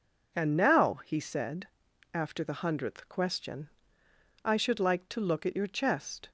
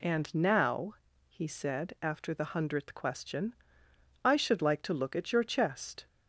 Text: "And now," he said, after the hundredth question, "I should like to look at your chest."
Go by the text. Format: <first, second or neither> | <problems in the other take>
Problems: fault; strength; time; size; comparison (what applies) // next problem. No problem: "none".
neither | none